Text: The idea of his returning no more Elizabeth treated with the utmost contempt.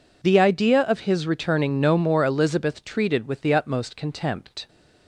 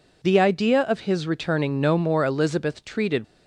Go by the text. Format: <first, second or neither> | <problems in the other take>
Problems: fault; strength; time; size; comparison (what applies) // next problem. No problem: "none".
first | stops before "with the utmost contempt"; at 3.2 s